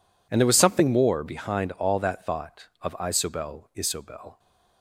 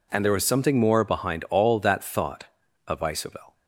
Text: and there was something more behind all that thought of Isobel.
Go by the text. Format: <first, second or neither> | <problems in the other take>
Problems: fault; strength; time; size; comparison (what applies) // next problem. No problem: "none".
second | says "Isobel" twice; at 3.7 s